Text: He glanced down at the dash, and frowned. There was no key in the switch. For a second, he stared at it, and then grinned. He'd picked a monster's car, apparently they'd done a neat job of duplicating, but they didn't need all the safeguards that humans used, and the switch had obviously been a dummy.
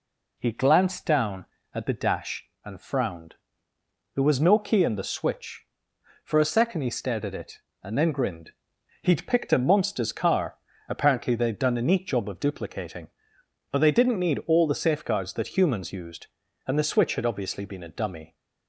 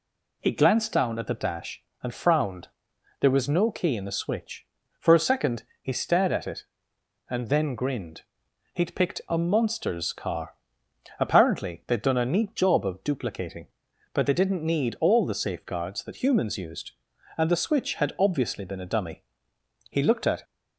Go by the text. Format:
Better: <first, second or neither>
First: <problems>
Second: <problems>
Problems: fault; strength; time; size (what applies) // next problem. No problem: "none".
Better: first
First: none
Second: goes on to say "He looked at"; from 19.8 s on; 0.54 s long